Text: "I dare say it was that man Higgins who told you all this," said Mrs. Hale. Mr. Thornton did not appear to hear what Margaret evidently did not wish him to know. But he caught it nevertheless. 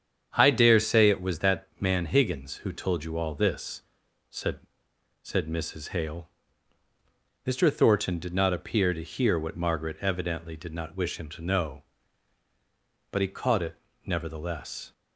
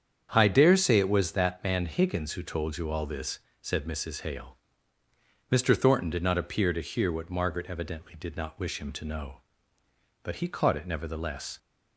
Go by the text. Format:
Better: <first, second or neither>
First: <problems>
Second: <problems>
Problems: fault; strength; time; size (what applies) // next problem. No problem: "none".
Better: second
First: starts louder than the rest; strong; until 1.3 s; 8 dB // says "said" twice; at 5.2 s // pauses between "it" and "nevertheless"; slight; at 13.7 s; 0.32 s long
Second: starts louder than the rest; strong; until 1.3 s; 8 dB